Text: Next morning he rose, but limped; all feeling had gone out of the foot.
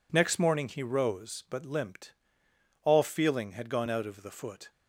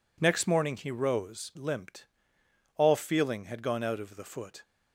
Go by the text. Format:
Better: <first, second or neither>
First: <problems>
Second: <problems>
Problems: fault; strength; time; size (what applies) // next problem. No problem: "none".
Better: first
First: none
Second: skips "but"; at 1.5 s